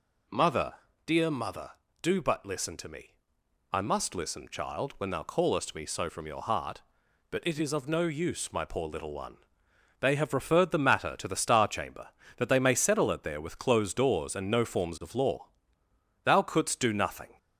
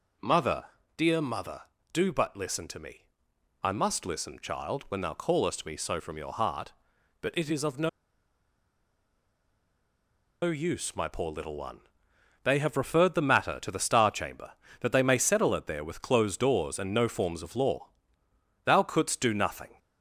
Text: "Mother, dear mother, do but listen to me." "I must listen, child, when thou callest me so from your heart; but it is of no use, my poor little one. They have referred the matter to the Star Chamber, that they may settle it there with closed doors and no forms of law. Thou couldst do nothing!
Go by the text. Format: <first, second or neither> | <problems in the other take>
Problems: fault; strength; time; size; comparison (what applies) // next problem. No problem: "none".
first | pauses between "no" and "use"; strong; at 7.8 s; 2.5 s long